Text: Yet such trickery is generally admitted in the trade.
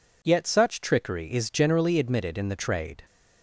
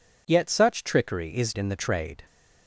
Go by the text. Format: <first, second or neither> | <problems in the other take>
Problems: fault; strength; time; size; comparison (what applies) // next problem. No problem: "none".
first | skips "generally admitted"; at 1.5 s